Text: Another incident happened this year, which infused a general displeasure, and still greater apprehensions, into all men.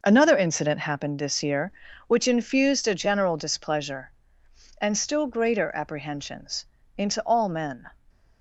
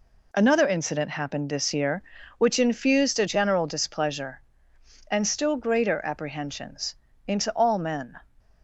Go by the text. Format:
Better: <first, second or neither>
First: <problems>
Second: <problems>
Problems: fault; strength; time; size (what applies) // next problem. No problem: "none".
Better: second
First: starts louder than the rest; noticeable; until 1.0 s; 5.5 dB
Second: none